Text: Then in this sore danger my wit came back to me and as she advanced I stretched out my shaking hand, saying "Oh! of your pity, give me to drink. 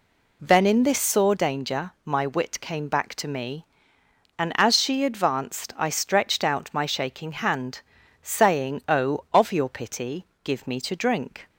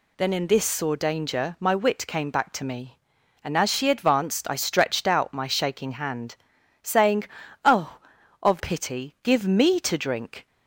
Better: first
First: none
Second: pauses between "saying" and "Oh"; at 7.2 s; 0.40 s long // skips "your"; at 8.5 s

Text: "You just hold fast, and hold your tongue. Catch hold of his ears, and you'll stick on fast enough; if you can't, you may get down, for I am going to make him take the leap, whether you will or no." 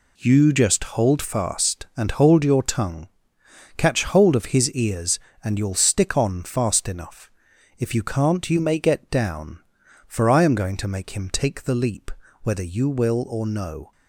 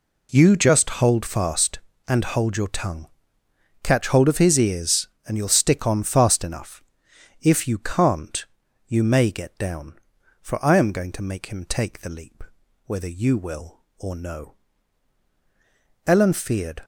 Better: first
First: none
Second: goes on to say "Ellen feared"; noticeable; from 16.0 s on; 0.76 s long

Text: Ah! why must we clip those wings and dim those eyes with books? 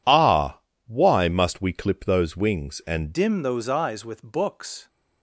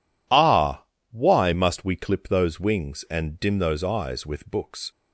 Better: second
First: changes voice at "dim"; from 3.1 s on; 1.7 s long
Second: none

